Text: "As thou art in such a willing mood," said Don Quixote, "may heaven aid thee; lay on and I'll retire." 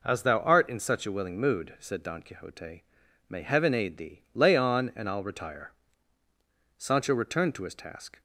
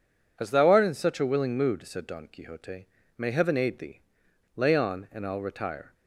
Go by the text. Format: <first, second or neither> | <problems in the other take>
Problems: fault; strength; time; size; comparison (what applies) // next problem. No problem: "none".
second | goes on to say "Sancho returned to his task"; from 6.7 s on; 1.4 s long